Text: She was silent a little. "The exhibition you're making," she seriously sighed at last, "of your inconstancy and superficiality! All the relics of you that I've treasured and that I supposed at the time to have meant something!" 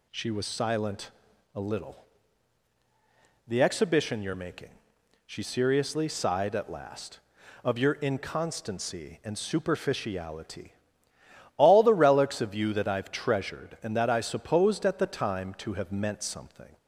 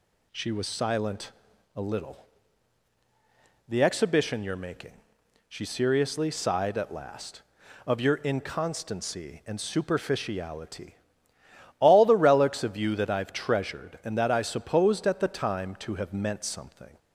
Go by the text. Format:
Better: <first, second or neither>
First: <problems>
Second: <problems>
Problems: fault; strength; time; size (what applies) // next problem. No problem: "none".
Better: neither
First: pauses between "silent" and "a"; at 1.1 s; 0.44 s long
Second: pauses between "silent" and "a"; at 1.3 s; 0.44 s long